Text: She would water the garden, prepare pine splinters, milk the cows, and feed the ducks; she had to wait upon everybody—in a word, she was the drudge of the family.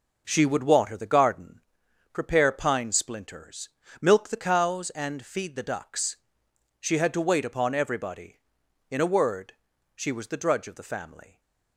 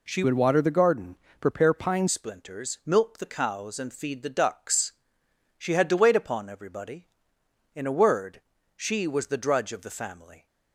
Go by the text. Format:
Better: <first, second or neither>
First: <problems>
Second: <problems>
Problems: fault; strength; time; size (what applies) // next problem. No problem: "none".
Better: first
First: none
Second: changes voice from "would" to "pine"; from 0.2 to 2.0 s; 1.8 s long